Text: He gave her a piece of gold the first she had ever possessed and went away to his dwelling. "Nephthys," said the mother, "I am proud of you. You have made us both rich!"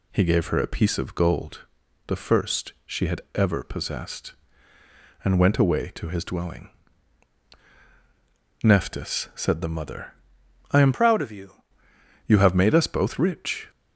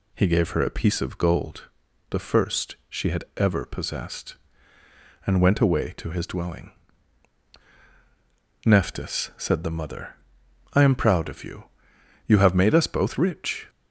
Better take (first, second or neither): second